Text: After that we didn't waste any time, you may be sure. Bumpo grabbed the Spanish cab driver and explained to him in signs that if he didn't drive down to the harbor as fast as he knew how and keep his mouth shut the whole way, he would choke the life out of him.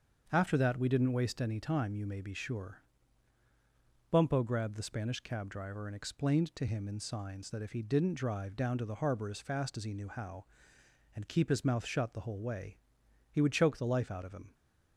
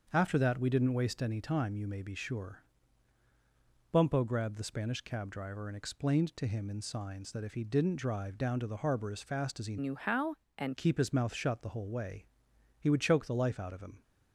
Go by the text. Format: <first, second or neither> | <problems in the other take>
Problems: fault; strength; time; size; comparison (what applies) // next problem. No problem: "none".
first | starts louder than the rest; until 1.1 s; 7 dB; also in the first // changes voice from "knew" to "and"; from 9.7 to 10.7 s; 1.0 s long